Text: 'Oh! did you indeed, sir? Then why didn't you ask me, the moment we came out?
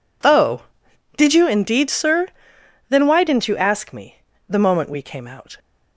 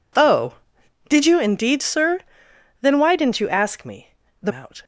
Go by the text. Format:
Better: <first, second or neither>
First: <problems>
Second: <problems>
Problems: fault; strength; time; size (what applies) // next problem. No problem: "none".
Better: first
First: none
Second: skips "moment we came"; at 4.5 s